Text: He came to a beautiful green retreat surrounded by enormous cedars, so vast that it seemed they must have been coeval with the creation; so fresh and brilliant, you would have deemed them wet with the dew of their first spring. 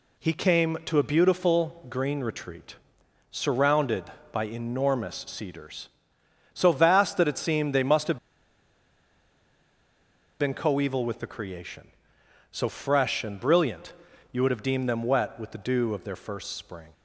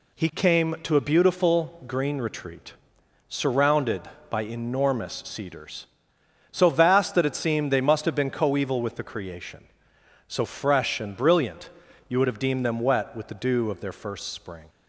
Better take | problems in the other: second | pauses between "retreat" and "surrounded"; noticeable; at 2.7 s; 0.54 s long; noticeable in the second // pauses between "have" and "been"; strong; at 8.1 s; 2.2 s long

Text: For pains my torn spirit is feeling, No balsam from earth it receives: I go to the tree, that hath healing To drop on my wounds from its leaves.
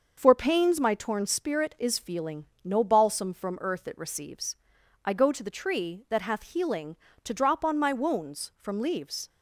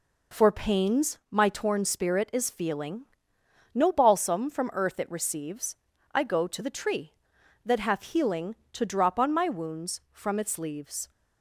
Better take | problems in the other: second | starts louder than the rest; until 1.1 s; 6 dB // skips "its"; at 8.8 s

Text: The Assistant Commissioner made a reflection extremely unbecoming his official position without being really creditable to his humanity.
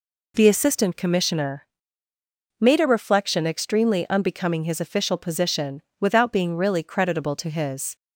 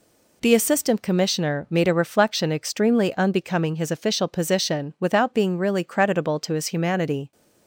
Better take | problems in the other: second | pauses between "Commissioner" and "made"; noticeable; at 1.6 s; 0.94 s long // pauses between "position" and "without"; slight; at 5.8 s; 0.20 s long // stops before "humanity"; at 7.9 s

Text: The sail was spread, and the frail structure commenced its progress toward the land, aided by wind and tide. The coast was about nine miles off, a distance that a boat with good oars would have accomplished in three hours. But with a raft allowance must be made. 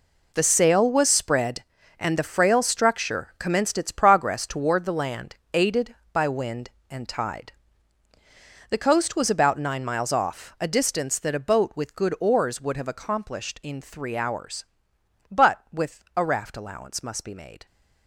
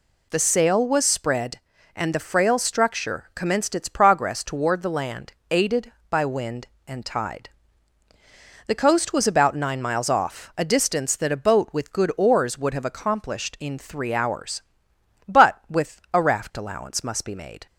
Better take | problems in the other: second | gets quieter; strong; throughout; 12 dB

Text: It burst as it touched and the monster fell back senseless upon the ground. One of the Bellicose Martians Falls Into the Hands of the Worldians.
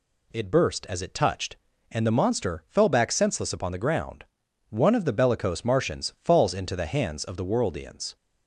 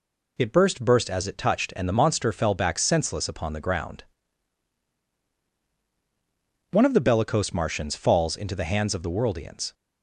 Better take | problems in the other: first | says "burst" twice; at 0.8 s

